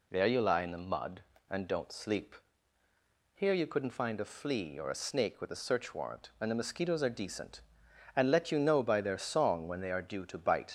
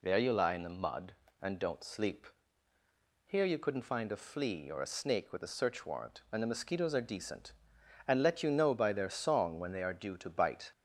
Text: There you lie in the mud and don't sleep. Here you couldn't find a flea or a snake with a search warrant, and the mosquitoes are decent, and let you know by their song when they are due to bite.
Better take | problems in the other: second | leaves "bite" unfinished; at 10.6 s; 55 ms

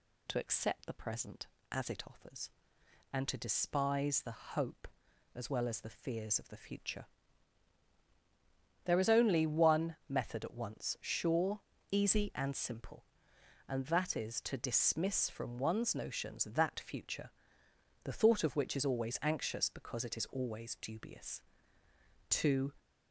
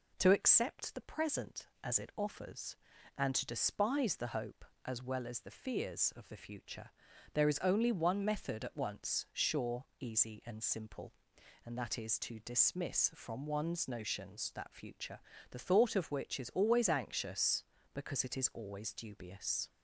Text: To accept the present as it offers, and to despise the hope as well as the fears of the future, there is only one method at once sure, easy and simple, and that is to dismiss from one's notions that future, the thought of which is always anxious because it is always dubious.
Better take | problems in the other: second | goes on to say "To"; slight; from 22.3 s on; 0.42 s long

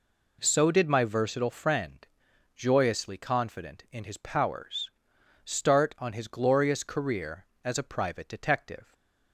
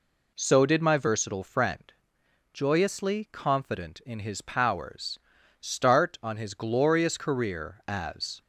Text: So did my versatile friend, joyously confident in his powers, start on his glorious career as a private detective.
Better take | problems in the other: first | stops before "a private detective"; at 8.4 s

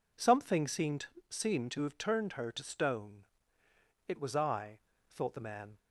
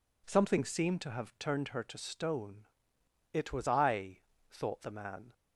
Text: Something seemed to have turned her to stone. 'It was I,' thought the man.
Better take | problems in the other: second | says "seemed" twice; at 1.2 s

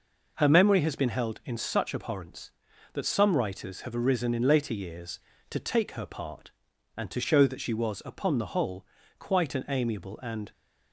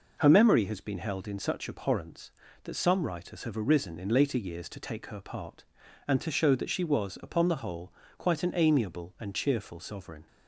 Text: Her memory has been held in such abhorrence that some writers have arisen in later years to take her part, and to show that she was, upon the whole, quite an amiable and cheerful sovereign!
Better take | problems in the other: second | stops before "cheerful sovereign"; at 10.5 s

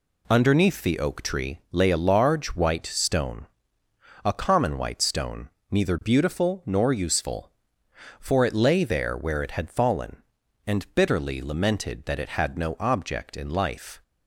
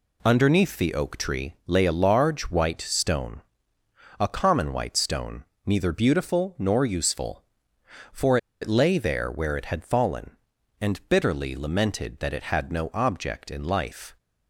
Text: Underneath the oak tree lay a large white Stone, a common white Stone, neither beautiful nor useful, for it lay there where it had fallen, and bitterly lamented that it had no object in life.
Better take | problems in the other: first | pauses between "for" and "it"; slight; at 8.3 s; 0.24 s long

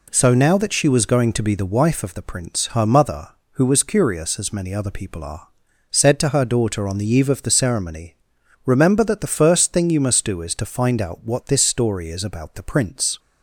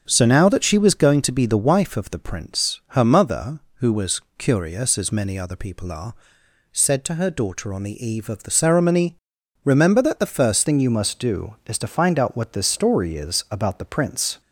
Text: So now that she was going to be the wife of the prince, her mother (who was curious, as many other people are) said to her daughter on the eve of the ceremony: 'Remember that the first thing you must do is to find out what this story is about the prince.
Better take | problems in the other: first | starts louder than the rest; strong; until 1.0 s; 7 dB // pauses between "was" and "curious"; slight; at 4.2 s; 0.18 s long // changes voice at "thing"; from 10.6 s on; 3.7 s long

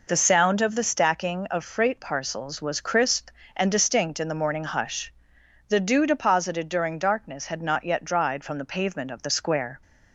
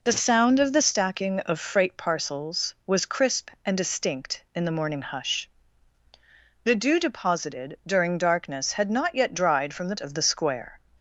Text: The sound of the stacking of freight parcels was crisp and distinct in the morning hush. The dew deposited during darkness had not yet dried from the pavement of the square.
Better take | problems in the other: first | skips "pavement"; at 9.9 s

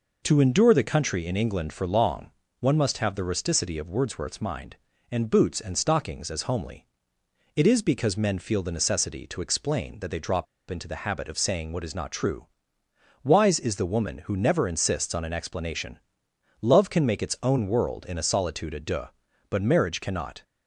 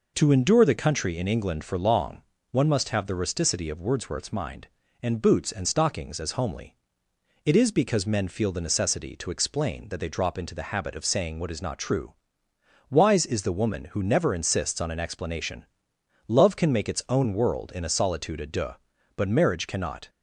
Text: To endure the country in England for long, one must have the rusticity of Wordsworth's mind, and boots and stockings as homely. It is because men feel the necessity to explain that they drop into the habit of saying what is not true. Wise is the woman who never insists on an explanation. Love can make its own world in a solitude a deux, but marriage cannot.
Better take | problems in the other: second | pauses between "drop" and "into"; slight; at 10.4 s; 0.25 s long

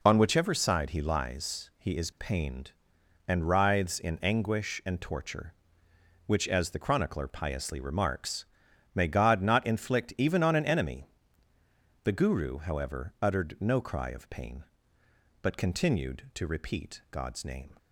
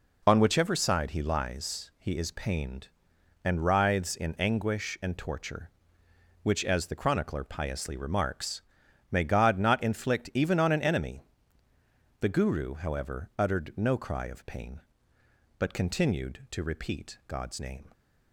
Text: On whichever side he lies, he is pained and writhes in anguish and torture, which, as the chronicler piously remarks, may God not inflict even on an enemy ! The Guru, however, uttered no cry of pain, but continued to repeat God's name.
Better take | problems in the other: neither | none

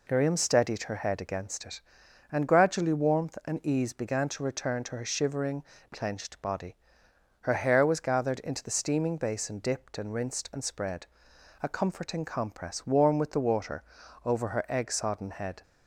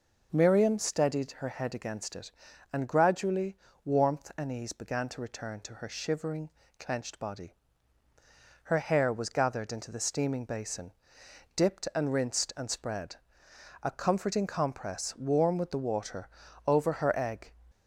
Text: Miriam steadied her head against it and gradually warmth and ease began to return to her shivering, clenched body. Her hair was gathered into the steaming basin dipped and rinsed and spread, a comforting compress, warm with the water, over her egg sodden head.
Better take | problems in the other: first | pauses between "gradually" and "warmth"; slight; at 3.5 s; 0.28 s long // pauses between "basin" and "dipped"; noticeable; at 10.9 s; 0.64 s long // stops before "sodden head"; at 17.7 s

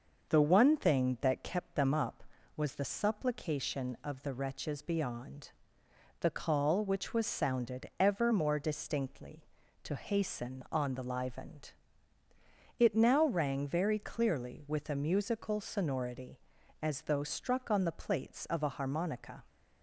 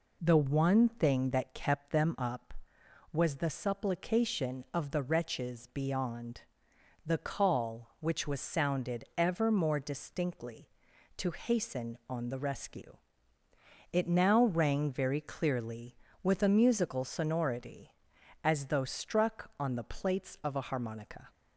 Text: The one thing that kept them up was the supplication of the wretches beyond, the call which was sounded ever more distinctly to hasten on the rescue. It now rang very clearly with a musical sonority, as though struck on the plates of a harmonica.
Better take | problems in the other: second | starts louder than the rest; until 1.3 s; 6 dB // says "livened" for "rescue"; at 11.0 s

